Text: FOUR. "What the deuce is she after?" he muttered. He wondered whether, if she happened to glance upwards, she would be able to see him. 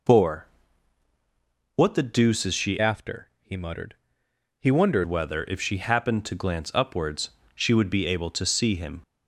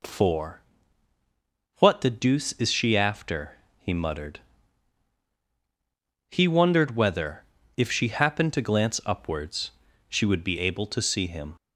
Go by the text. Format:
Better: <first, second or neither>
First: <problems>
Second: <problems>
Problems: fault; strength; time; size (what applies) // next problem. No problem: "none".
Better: second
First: changes voice from "after" to "wondered"; from 2.7 to 5.0 s; 2.3 s long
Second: none